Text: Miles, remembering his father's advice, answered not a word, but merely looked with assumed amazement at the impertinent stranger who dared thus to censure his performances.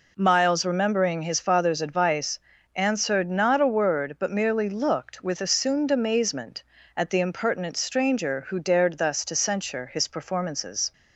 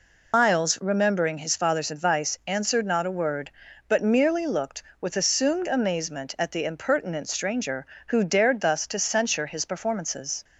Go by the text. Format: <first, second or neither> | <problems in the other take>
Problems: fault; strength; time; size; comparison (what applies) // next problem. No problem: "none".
first | loses the start of "Miles"; at 0.3 s; 130 ms